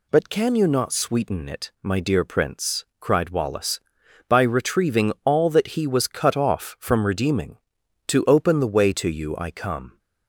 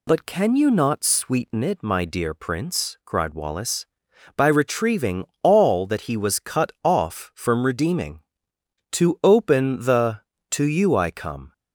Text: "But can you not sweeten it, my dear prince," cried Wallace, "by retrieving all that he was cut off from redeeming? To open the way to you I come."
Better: first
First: none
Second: pauses between "retrieving" and "all"; slight; at 5.2 s; 0.16 s long // skips "way"; at 10.3 s

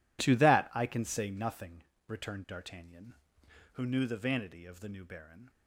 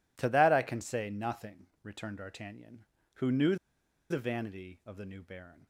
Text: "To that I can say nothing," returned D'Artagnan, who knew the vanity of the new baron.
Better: first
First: none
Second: pauses between "knew" and "the"; noticeable; at 3.5 s; 0.54 s long

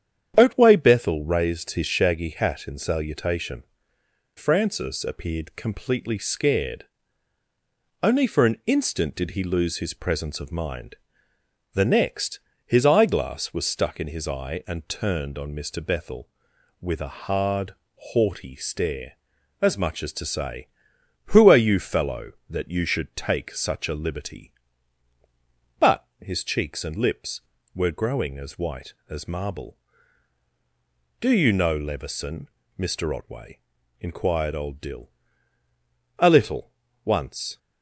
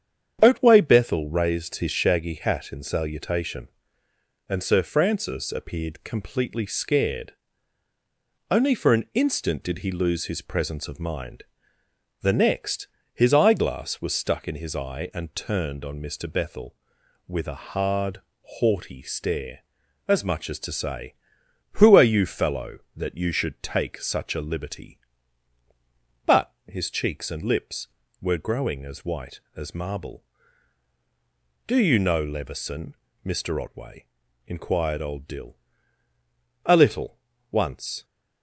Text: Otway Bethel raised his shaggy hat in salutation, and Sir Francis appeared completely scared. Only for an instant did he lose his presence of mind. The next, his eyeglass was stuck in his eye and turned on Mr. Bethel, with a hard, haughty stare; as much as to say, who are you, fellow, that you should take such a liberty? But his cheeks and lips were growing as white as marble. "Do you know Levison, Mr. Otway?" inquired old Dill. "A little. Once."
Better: second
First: starts louder than the rest; strong; until 1.3 s; 9 dB // skips "and Sir"; at 3.9 s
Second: starts louder than the rest; strong; until 1.4 s; 8.5 dB

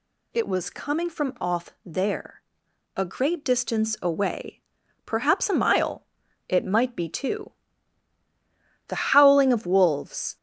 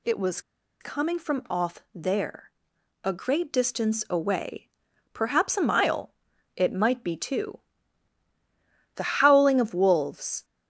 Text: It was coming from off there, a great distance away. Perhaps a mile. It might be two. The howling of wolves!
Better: first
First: none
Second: pauses between "was" and "coming"; at 0.4 s; 0.40 s long

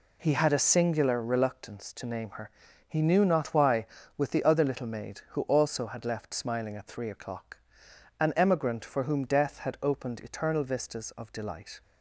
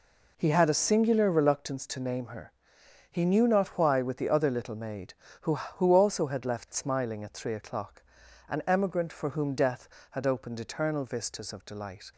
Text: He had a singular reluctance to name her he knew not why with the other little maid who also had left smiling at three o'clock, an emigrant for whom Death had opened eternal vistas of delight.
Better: first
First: pauses between "her" and "he"; slight; at 2.4 s; 0.36 s long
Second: pauses between "her" and "he"; noticeable; at 2.5 s; 0.58 s long // says "who" twice; at 5.5 s

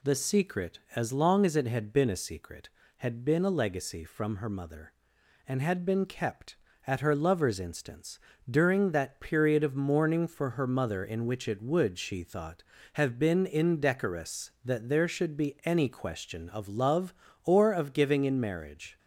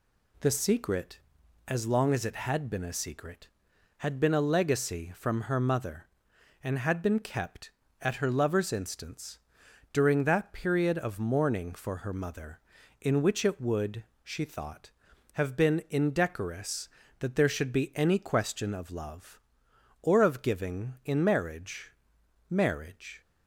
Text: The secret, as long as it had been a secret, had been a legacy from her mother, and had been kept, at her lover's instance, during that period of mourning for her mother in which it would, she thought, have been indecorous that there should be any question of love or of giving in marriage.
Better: first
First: none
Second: says "marriage" twice; at 22.5 s

